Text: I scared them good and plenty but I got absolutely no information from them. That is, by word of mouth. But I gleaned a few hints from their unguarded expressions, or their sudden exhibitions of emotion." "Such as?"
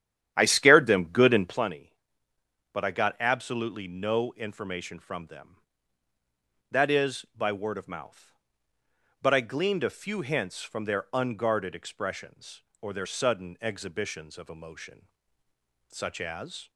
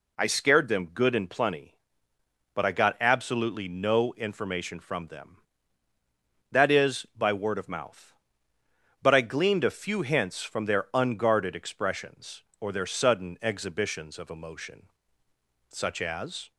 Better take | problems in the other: second | starts louder than the rest; strong; until 1.7 s; 10.5 dB

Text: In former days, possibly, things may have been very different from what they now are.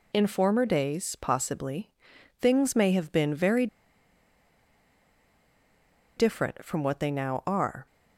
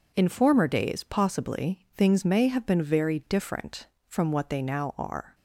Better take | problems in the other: second | pauses between "very" and "different"; strong; at 3.6 s; 2.5 s long

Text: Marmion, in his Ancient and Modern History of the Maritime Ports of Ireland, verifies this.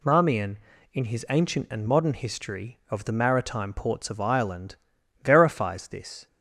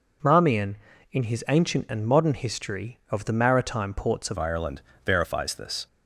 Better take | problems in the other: first | changes voice at "Ireland"; from 4.3 s on; 1.5 s long

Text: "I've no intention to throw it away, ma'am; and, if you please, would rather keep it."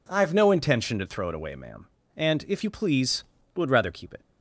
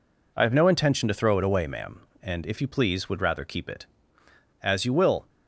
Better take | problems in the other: first | goes on to say "As you will"; noticeable; from 4.6 s on; 0.64 s long

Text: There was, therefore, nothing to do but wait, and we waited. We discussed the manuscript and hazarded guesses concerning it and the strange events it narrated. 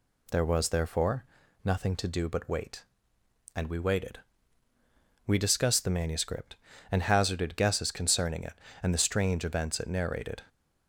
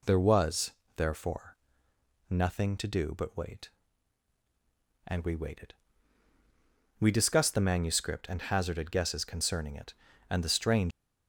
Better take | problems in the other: first | stops before "events it narrated"; at 10.9 s

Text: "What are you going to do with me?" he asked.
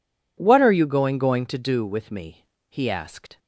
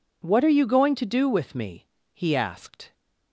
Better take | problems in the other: second | says "going" twice; at 1.1 s

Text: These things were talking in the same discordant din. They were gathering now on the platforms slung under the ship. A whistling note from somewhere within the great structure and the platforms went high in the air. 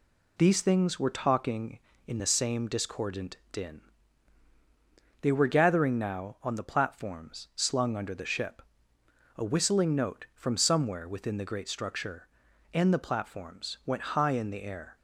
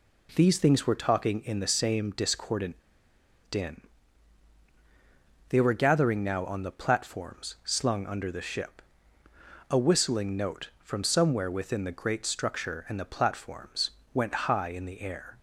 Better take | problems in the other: first | pauses between "discordant" and "din"; noticeable; at 2.7 s; 0.74 s long // pauses between "platforms" and "went"; slight; at 13.9 s; 0.20 s long

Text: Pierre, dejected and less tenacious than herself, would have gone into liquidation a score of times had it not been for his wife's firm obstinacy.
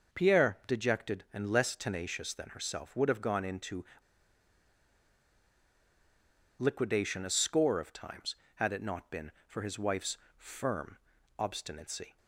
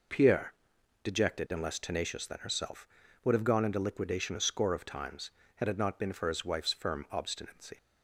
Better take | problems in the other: second | pauses between "into" and "liquidation"; strong; at 3.8 s; 2.7 s long // pauses between "wife's" and "firm"; slight; at 10.1 s; 0.20 s long // pauses between "firm" and "obstinacy"; at 10.9 s; 0.42 s long

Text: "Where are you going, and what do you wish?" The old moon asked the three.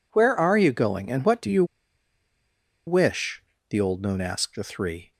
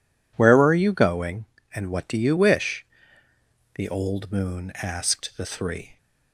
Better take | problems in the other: second | pauses between "you" and "wish"; at 1.6 s; 1.2 s long

